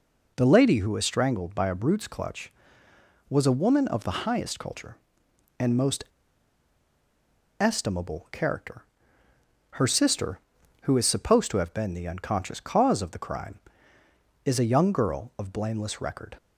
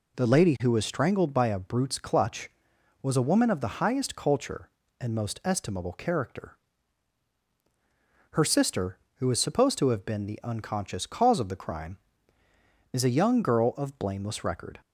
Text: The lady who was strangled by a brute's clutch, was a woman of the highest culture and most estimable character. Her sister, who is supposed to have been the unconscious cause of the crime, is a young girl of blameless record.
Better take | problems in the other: second | pauses between "most" and "estimable"; strong; at 6.0 s; 1.5 s long

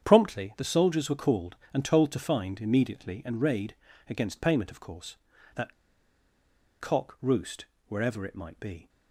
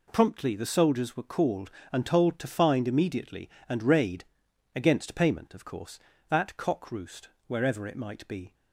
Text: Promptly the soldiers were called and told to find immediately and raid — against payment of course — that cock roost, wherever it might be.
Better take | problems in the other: second | starts louder than the rest; strong; until 1.0 s; 8.5 dB // pauses between "that" and "cock"; at 5.7 s; 1.0 s long

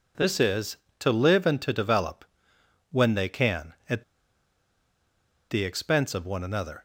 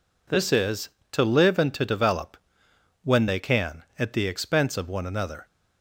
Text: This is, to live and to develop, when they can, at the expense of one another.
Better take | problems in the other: second | pauses between "at" and "the"; strong; at 4.0 s; 1.4 s long

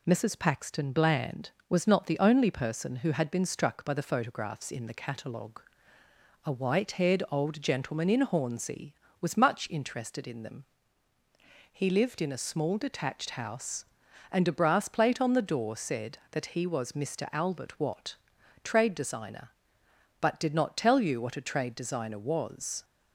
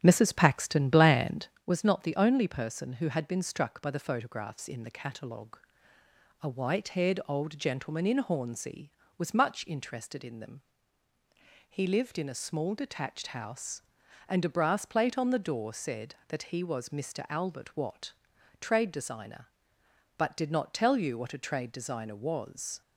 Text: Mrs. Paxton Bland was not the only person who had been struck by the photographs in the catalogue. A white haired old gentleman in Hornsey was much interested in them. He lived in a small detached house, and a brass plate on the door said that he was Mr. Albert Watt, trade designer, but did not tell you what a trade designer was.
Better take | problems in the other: first | starts louder than the rest; strong; until 1.7 s; 9 dB

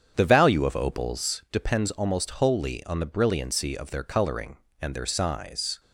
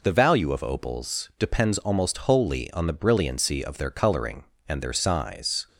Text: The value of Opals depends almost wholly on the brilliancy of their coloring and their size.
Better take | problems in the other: second | starts louder than the rest; strong; until 1.5 s; 8 dB

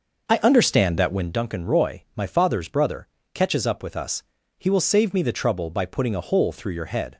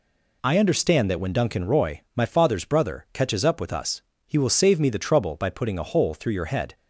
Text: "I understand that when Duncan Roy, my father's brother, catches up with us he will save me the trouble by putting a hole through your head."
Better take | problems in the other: second | starts louder than the rest; noticeable; until 1.4 s; 6 dB // pauses between "us" and "he"; slight; at 4.2 s; 0.36 s long; slight in the second

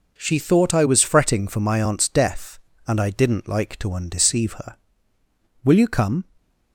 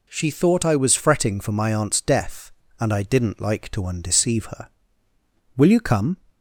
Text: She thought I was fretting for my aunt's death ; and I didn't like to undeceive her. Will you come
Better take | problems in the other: second | gets quieter; strong; throughout; 8.5 dB // stays silent after the last word; slight; from 6.2 s on; 0.5 s long

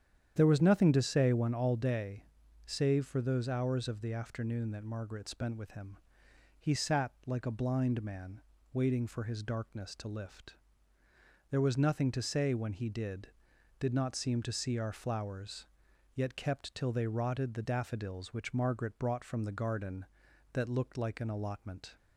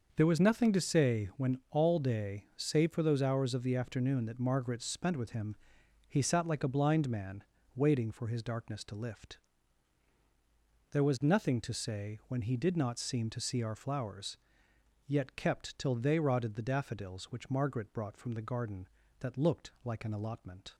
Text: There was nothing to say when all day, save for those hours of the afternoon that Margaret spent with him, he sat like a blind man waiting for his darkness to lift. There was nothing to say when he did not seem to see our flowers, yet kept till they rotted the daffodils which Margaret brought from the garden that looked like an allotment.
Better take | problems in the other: second | starts louder than the rest; strong; until 1.3 s; 9 dB; also in the second // pauses between "man" and "waiting"; slight; at 8.4 s; 0.30 s long; slight in the second // says "did" twice; at 13.7 s

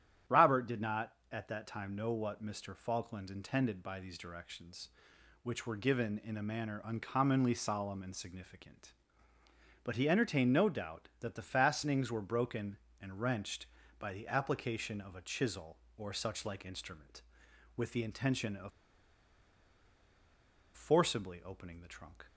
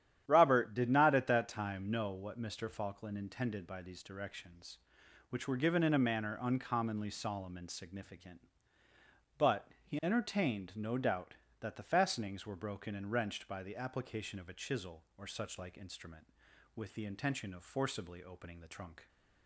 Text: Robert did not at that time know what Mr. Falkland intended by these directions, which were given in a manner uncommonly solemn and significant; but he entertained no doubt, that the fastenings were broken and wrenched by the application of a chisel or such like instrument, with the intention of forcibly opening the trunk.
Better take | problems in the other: second | starts louder than the rest; strong; until 1.4 s; 10.5 dB; strong in the second // pauses between "of" and "forcibly"; strong; at 18.7 s; 2.0 s long

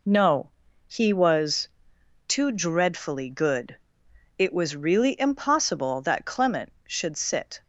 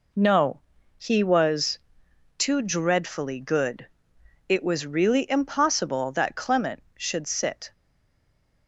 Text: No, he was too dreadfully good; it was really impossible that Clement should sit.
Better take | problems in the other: first | pauses between "was" and "too"; noticeable; at 1.7 s; 0.58 s long; noticeable in the first // stays silent after the last word; slight; from 7.7 s on; 0.9 s long

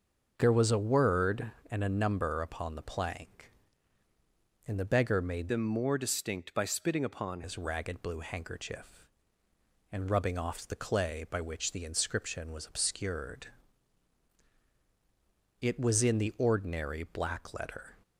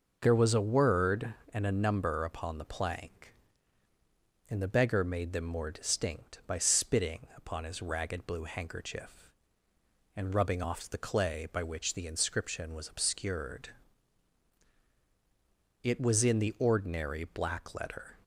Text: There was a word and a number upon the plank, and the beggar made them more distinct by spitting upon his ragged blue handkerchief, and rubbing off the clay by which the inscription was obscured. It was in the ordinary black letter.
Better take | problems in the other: second | starts louder than the rest; until 1.3 s; 6.5 dB // changes voice from "them" to "upon"; from 5.4 to 7.4 s; 2.0 s long

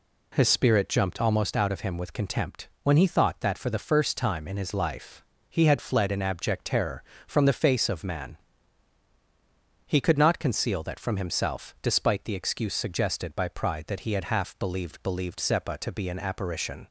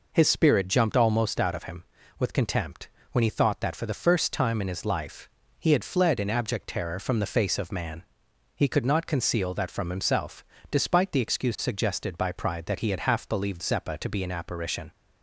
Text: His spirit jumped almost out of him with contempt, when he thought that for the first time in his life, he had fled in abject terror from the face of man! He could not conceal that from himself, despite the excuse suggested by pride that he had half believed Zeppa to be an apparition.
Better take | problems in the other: second | says "believed" twice; at 15.0 s

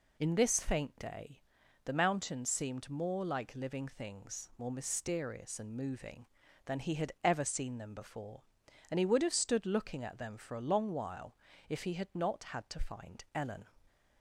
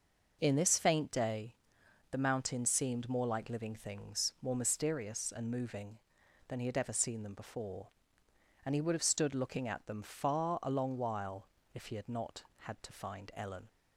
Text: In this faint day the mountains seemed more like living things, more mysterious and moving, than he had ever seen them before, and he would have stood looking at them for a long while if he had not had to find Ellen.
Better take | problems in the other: first | pauses between "day" and "the"; noticeable; at 1.5 s; 0.58 s long; also in the first // says "far" for "for"; at 10.0 s // pauses between "while" and "if"; slight; at 11.4 s; 0.28 s long; slight in the first

